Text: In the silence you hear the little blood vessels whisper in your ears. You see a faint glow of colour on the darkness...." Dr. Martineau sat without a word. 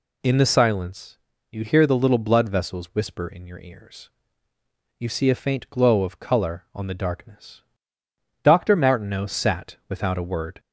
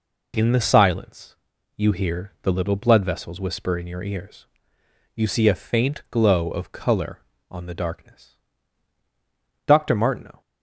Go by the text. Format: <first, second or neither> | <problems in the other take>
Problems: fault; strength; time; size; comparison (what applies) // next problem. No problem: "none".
first | pauses between "silence" and "you"; at 1.3 s; 0.40 s long; slight in the first // stops before "sat without a word"; at 10.4 s